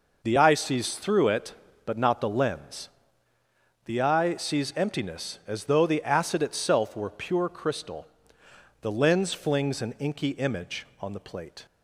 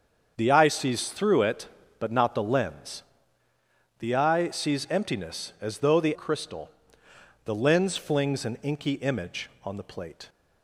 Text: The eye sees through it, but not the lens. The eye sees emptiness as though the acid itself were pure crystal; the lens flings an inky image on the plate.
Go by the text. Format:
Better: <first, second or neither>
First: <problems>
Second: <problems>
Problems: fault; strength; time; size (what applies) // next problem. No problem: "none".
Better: first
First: none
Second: starts louder than the rest; until 1.3 s; 7 dB // skips "acid itself were pure"; at 6.1 s